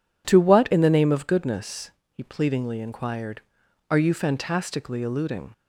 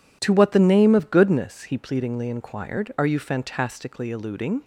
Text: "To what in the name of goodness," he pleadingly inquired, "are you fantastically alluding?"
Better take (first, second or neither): first